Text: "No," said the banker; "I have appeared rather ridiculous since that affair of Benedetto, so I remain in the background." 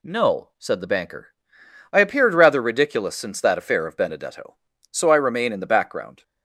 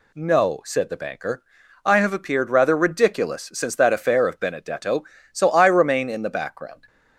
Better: second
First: skips "have"; at 1.9 s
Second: none

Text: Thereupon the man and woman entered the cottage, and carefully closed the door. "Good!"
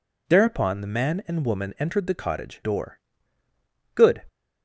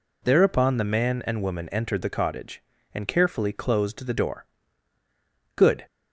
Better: second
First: skips "and carefully closed the"; at 2.6 s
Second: none

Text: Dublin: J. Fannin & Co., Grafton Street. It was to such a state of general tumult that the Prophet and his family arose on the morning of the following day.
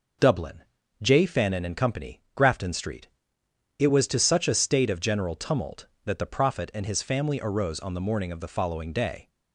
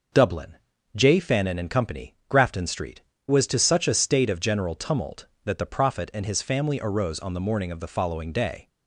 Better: first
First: none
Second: skips "It"; at 3.1 s

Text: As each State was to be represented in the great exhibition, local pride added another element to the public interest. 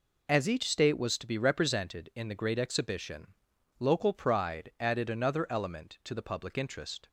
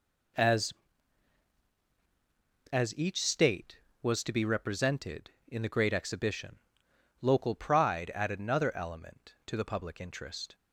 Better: first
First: none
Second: says "As" twice; at 2.7 s

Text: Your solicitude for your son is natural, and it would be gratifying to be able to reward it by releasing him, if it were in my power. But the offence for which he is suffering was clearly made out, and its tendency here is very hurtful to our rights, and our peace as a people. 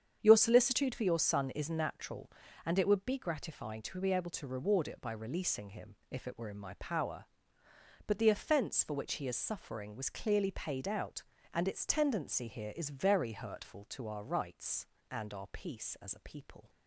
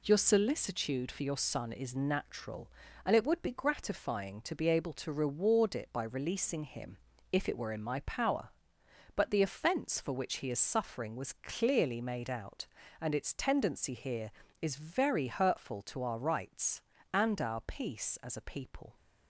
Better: second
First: starts louder than the rest; strong; until 1.2 s; 8 dB // says "paid" for "made"; at 10.4 s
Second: none

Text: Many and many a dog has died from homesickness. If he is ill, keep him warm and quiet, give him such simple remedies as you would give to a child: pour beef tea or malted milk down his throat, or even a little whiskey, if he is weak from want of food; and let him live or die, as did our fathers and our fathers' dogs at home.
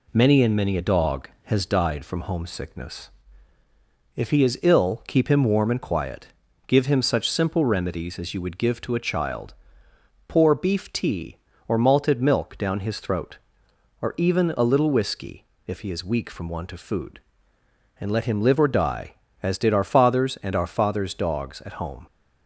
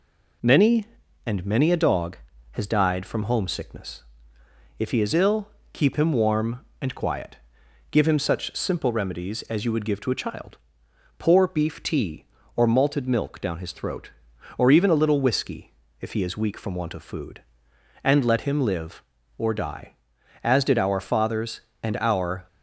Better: first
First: none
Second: stops before "fathers dogs at home"; at 22.4 s

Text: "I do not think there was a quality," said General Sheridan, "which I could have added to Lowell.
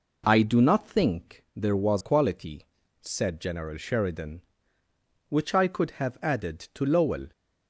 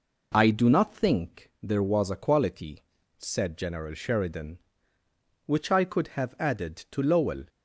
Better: second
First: skips "a"; at 2.0 s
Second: none

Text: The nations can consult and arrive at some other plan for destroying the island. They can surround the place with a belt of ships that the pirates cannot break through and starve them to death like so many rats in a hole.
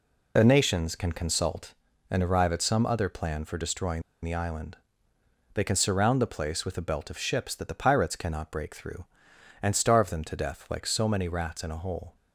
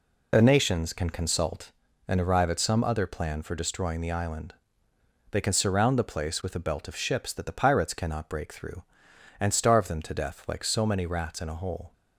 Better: second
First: pauses between "destroying" and "the"; slight; at 4.0 s; 0.21 s long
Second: none

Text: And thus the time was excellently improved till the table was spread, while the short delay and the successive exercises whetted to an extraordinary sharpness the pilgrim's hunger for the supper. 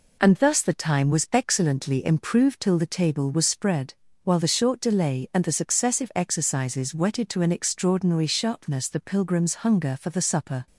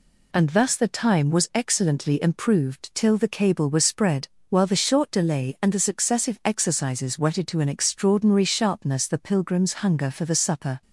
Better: first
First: none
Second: says "cable" for "table"; at 3.2 s

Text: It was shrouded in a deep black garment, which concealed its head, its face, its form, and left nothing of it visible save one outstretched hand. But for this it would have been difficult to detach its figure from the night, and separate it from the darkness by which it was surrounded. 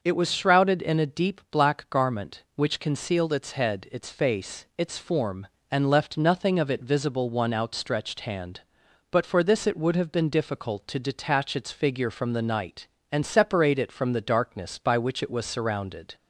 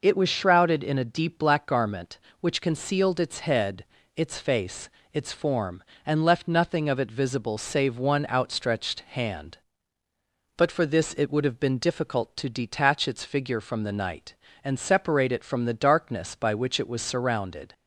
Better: second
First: skips "save"; at 7.2 s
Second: none

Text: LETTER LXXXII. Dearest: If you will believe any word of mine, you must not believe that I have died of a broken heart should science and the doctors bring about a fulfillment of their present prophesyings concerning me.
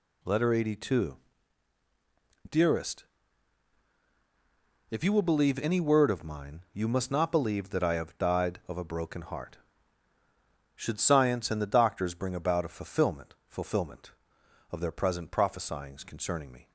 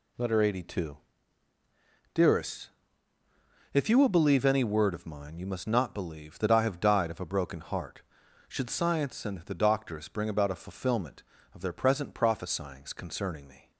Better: second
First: says "fulfillment" twice; at 13.4 s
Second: none

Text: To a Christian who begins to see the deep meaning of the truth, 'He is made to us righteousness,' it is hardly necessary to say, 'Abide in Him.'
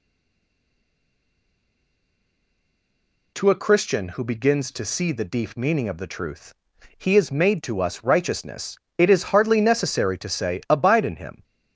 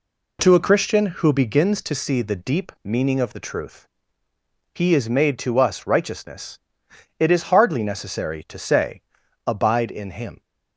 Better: second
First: stays silent before the first word; strong; until 3.3 s; 3.3 s long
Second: none

